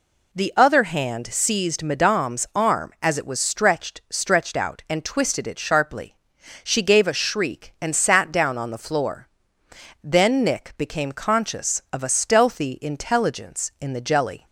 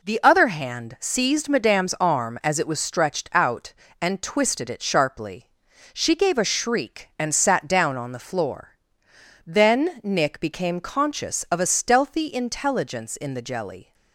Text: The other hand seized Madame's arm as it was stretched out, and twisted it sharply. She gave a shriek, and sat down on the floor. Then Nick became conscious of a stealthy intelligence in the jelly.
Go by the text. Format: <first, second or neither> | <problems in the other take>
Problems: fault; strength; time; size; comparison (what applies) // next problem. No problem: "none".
second | says "stretched" twice; at 4.0 s